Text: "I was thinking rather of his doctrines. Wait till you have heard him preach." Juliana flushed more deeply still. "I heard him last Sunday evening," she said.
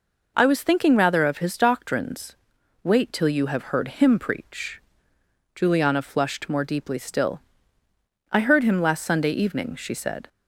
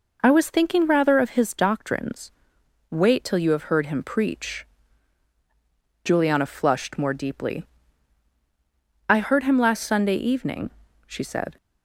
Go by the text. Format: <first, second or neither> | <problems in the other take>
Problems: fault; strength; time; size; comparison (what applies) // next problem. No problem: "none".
first | skips "still"; at 8.3 s